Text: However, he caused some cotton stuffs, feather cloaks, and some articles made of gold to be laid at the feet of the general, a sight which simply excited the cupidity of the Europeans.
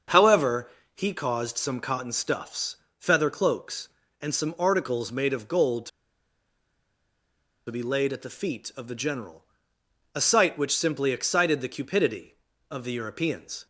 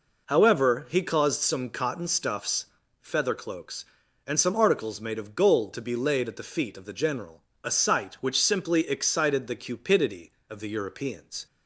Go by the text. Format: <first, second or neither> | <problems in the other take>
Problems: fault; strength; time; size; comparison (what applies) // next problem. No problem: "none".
second | starts louder than the rest; until 1.3 s; 6.5 dB // pauses between "to" and "be"; strong; at 5.8 s; 1.7 s long